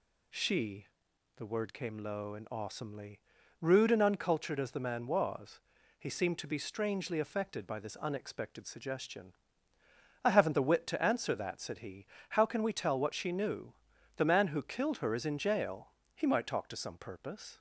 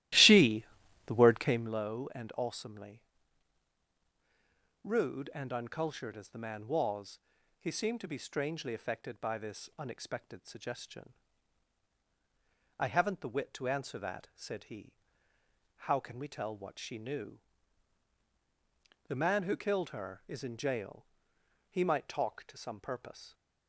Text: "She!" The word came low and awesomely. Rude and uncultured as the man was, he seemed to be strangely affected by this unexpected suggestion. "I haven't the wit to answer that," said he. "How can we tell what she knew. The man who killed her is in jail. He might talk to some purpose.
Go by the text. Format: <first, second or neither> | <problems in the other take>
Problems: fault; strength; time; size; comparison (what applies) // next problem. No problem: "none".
first | starts louder than the rest; strong; until 1.7 s; 15.5 dB